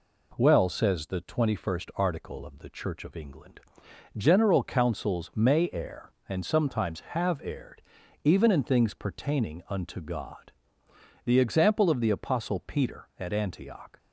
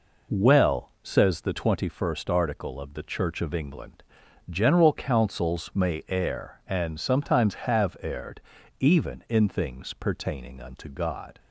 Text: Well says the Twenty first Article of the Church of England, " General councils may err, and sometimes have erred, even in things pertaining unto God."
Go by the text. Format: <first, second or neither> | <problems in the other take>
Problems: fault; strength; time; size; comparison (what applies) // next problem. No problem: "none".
second | goes on to say "The example of the Apostle Peter at Antioch"; strong; from 11.2 s on; 2.7 s long